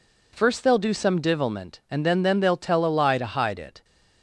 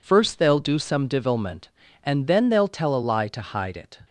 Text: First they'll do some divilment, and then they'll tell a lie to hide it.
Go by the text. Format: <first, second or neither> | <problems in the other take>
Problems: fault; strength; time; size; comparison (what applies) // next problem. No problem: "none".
second | says "then" twice; at 2.2 s